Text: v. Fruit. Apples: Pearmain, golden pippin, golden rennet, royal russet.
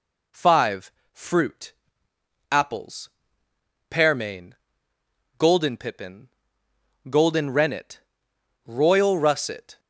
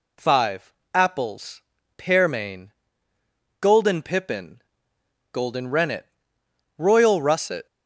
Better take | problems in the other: first | skips "Fruit"; at 0.8 s

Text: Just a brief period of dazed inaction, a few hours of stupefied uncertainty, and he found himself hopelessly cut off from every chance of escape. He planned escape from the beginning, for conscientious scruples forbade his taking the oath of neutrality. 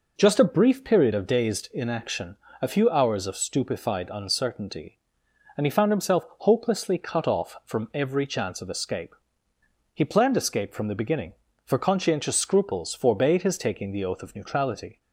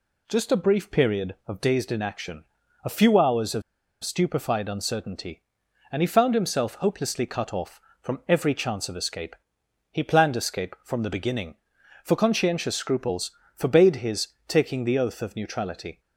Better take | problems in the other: first | pauses between "of" and "stupefied"; at 3.6 s; 0.41 s long // pauses between "scruples" and "forbade"; slight; at 13.2 s; 0.24 s long // pauses between "his" and "taking"; slight; at 14.2 s; 0.20 s long

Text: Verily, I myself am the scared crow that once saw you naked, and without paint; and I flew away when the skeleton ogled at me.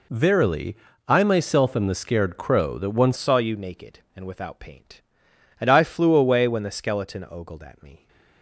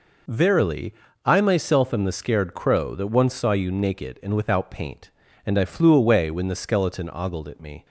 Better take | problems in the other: second | changes voice at "saw"; from 3.1 s on; 4.9 s long

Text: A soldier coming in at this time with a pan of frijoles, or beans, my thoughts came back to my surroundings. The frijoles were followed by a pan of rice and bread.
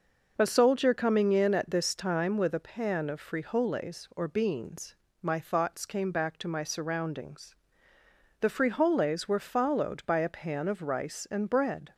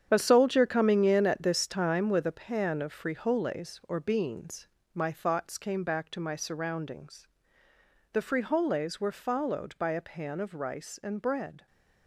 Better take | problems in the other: first | gets quieter; strong; throughout; 10.5 dB

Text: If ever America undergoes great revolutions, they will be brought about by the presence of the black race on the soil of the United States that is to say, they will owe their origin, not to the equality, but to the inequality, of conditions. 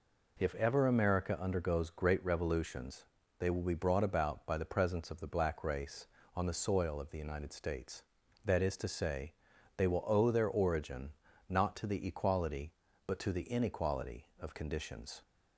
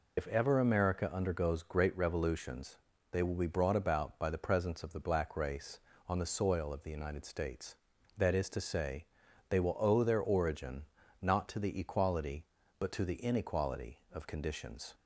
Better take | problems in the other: first | loses the start of "If"; at 0.1 s; 80 ms

